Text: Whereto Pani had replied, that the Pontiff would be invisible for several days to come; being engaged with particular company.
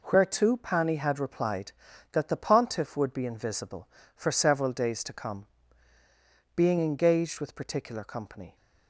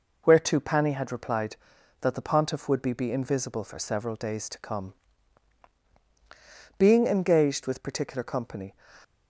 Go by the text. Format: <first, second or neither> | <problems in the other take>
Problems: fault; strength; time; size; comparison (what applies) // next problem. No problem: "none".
first | says "be" twice; at 2.9 s